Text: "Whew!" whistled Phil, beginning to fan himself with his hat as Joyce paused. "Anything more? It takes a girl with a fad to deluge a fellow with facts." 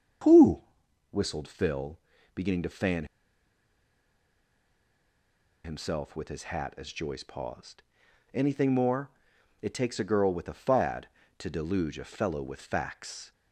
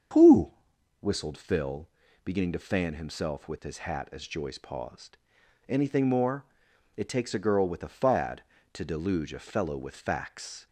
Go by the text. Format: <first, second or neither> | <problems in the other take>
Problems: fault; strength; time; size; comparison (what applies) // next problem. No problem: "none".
second | starts louder than the rest; strong; until 1.7 s; 7 dB; strong in the second // pauses between "fan" and "himself"; strong; at 3.0 s; 2.5 s long